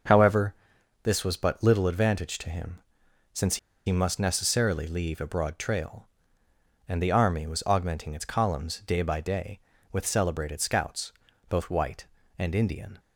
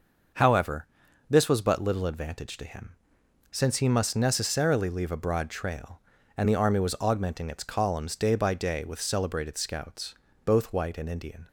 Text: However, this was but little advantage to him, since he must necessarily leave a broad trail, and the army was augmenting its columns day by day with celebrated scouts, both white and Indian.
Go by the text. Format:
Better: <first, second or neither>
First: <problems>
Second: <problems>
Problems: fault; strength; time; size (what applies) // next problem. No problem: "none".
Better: second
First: starts louder than the rest; noticeable; until 1.5 s; 6 dB // pauses between "since" and "he"; slight; at 3.5 s; 0.29 s long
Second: starts louder than the rest; noticeable; until 1.7 s; 6 dB